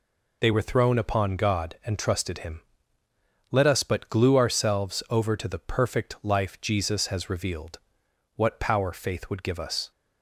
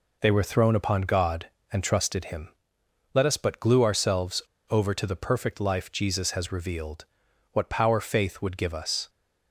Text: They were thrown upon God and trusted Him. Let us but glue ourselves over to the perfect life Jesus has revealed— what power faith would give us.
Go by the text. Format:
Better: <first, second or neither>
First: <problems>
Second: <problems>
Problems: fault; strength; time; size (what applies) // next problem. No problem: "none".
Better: first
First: none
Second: pauses between "ourselves" and "over"; slight; at 4.4 s; 0.28 s long